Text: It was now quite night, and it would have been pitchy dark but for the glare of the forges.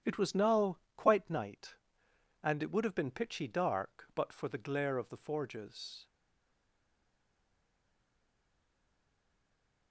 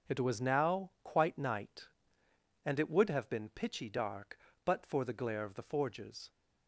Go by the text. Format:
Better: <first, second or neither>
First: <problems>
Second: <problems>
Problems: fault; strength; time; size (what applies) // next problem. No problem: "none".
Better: second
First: starts louder than the rest; strong; until 1.2 s; 10 dB // pauses between "now" and "quite"; slight; at 0.7 s; 0.20 s long // stays silent after the last word; strong; from 6.0 s on; 3.9 s long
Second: none